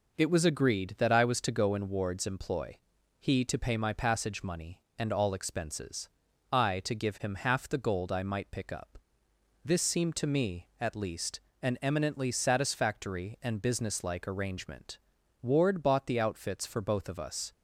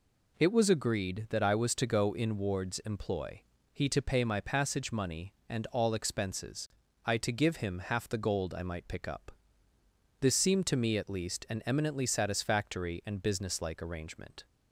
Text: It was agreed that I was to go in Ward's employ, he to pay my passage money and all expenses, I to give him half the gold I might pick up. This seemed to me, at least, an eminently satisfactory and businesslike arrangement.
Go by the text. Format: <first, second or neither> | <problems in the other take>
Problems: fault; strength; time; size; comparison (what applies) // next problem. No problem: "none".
second | goes on to say "Ward bought the outfits for both of us"; strong; from 15.4 s on; 2.1 s long